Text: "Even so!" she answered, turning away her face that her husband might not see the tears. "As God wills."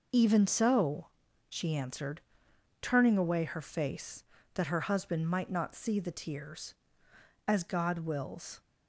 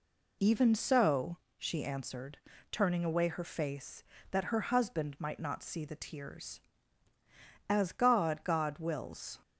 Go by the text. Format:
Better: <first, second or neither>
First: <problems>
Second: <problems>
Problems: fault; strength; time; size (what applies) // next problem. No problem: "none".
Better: first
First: none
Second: says "God" twice; at 8.4 s